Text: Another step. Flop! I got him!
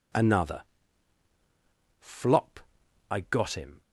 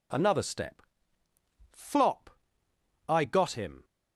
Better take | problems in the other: second | skips "step"; at 1.3 s

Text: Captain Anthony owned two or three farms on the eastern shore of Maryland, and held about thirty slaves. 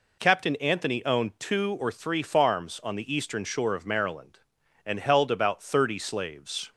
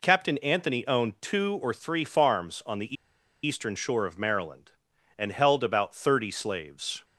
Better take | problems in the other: first | pauses between "the" and "eastern"; noticeable; at 2.9 s; 0.50 s long

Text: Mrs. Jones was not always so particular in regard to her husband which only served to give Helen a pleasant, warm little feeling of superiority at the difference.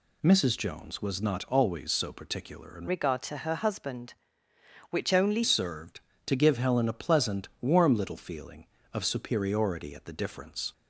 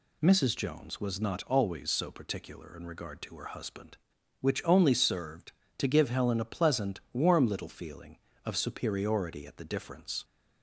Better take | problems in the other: second | changes voice from "regard" to "only"; from 2.8 to 5.4 s; 2.6 s long

